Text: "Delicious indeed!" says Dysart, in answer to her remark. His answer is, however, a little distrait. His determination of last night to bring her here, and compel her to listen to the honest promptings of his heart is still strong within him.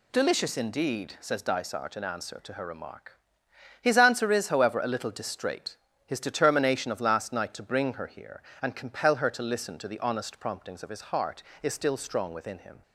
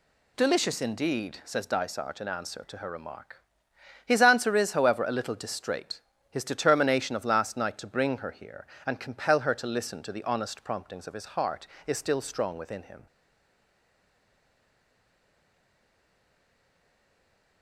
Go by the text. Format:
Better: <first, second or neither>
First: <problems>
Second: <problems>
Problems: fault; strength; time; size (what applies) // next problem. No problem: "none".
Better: first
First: none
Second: stays silent after the last word; strong; from 13.0 s on; 4.6 s long